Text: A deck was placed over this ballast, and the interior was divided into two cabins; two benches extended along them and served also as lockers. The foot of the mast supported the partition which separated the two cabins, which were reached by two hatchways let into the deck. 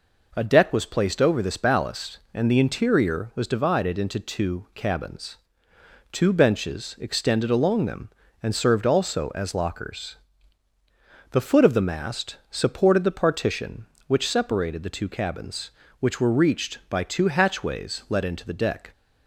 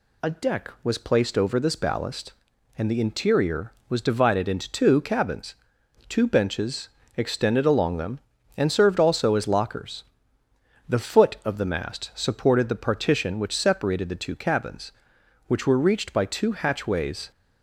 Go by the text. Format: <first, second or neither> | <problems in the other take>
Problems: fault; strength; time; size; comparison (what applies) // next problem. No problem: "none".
first | pauses between "benches" and "extended"; slight; at 6.8 s; 0.28 s long // stops before "let into the deck"; at 17.3 s